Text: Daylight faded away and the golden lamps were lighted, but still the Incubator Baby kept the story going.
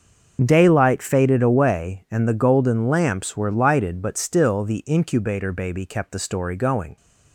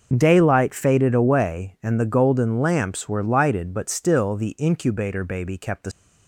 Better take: first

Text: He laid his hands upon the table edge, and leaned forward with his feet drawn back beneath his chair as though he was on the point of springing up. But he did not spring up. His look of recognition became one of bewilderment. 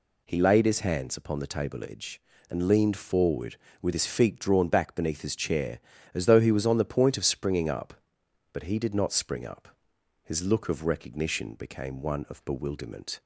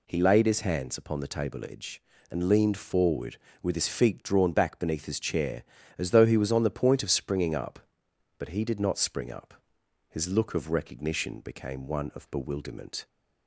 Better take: neither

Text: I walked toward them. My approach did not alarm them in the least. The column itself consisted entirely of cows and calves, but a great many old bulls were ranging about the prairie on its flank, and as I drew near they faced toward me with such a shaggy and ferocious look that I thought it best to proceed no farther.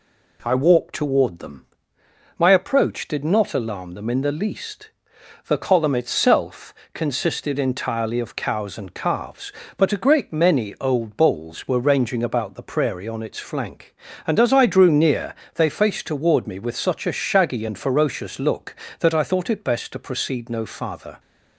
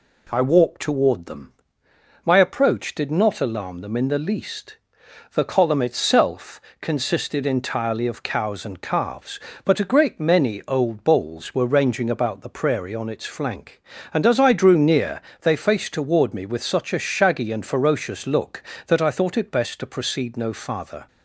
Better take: neither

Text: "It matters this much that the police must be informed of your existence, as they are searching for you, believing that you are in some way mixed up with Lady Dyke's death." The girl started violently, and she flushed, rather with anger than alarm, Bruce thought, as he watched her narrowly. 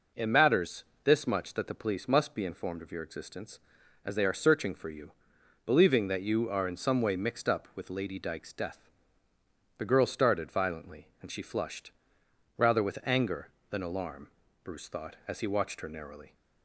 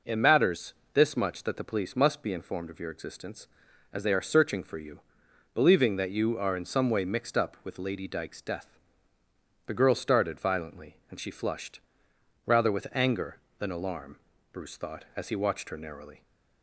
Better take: neither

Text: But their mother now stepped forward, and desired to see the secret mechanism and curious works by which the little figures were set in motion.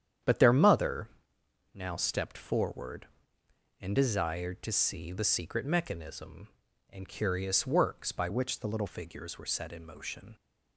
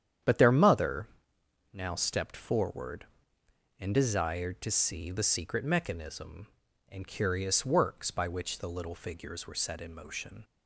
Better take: second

